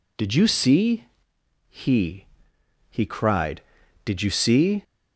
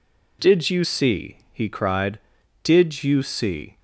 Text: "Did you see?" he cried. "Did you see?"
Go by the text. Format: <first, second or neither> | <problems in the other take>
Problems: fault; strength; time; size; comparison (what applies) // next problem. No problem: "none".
second | says "he" twice; at 2.8 s